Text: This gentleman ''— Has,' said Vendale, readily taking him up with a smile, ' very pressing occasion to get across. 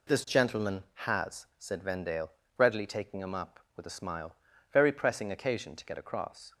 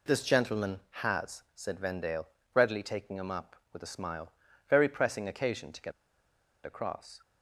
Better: first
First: none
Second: pauses between "get" and "across"; noticeable; at 5.9 s; 0.74 s long

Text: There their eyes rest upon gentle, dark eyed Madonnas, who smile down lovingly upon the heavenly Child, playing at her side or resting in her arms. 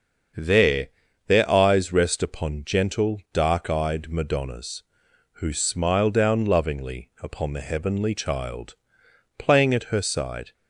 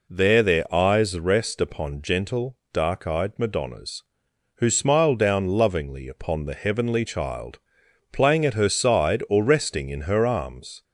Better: second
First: starts louder than the rest; until 1.7 s; 7 dB // pauses between "There" and "their"; at 0.8 s; 0.40 s long // stops before "or resting in her arms"; at 10.5 s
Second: none

